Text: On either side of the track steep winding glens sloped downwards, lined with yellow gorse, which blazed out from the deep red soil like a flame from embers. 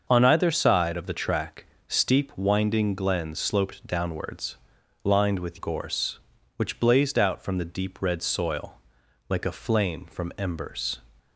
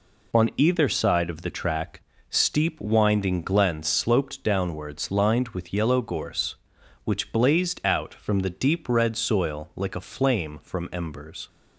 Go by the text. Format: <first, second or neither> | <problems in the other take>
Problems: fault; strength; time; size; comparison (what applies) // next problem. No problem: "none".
second | starts louder than the rest; until 1.1 s; 6.5 dB // pauses between "track" and "steep"; slight; at 1.6 s; 0.20 s long; slight in the second // skips "yellow"; at 5.5 s // pauses between "soil" and "like"; noticeable; at 8.7 s; 0.50 s long